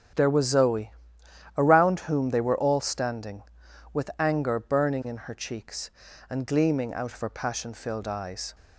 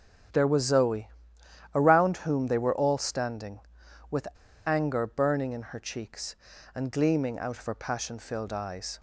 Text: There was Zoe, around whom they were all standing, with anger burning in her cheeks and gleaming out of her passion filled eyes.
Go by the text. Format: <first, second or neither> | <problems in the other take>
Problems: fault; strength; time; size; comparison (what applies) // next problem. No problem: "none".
first | starts louder than the rest; strong; until 1.9 s; 9.5 dB; strong in the first // pauses between "with" and "anger"; at 4.2 s; 0.37 s long